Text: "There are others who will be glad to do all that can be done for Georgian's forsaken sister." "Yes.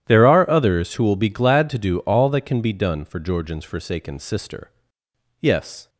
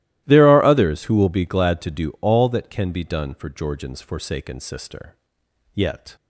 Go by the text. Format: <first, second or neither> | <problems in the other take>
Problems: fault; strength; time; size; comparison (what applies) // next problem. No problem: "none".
first | starts louder than the rest; strong; until 1.2 s; 16 dB; strong in the first // says "Yet" for "Yes"; at 5.7 s